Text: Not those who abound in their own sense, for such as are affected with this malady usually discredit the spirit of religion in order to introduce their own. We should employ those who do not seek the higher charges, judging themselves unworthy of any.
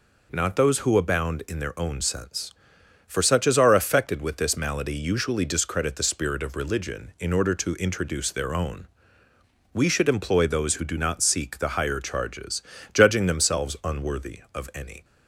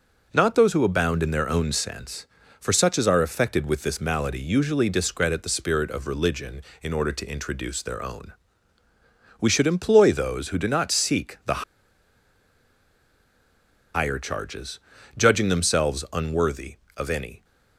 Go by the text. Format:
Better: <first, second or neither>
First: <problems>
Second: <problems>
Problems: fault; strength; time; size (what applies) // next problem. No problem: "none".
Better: first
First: none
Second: starts louder than the rest; noticeable; until 1.3 s; 6 dB // pauses between "the" and "higher"; strong; at 11.6 s; 2.3 s long